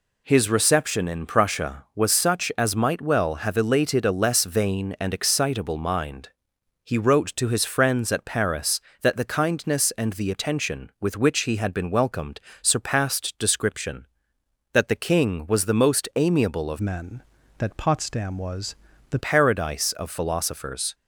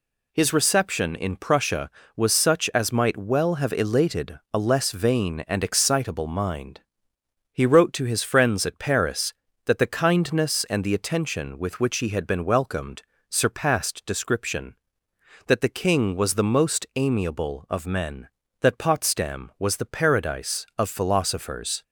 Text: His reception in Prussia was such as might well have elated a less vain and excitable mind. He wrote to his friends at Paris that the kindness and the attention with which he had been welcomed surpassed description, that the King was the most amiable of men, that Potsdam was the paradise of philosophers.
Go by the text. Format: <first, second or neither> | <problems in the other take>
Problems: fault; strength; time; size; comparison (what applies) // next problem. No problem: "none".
second | pauses between "welcomed" and "surpassed"; slight; at 12.3 s; 0.22 s long; slight in the second // changes voice from "men" to "the"; from 16.8 to 19.1 s; 2.3 s long // pauses between "was" and "the"; slight; at 18.7 s; 0.36 s long